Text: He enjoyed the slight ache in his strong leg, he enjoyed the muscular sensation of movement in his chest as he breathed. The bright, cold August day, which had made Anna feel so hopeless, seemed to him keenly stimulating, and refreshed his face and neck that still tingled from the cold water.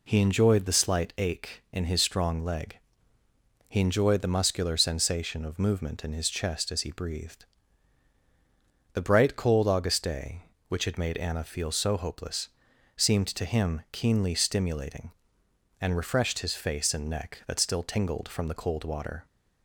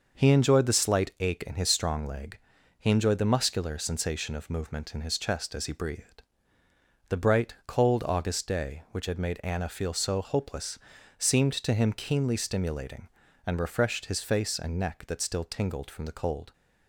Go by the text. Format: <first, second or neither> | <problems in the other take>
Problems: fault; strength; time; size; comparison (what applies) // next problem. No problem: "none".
first | starts louder than the rest; noticeable; until 1.2 s; 6 dB // stops before "water"; at 16.5 s